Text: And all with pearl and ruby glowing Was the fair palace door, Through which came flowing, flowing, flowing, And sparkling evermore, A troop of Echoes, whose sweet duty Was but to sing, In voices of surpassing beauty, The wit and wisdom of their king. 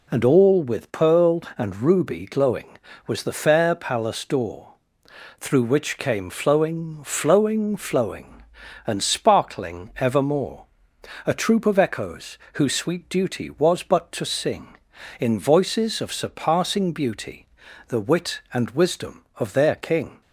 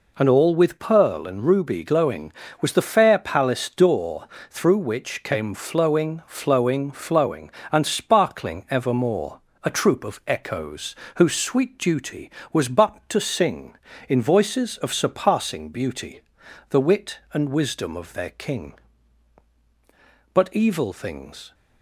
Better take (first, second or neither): first